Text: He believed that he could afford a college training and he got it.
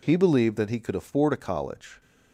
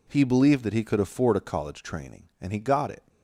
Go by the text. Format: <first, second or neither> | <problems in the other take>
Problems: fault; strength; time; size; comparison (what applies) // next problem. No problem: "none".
second | stops before "training and he got it"; at 2.0 s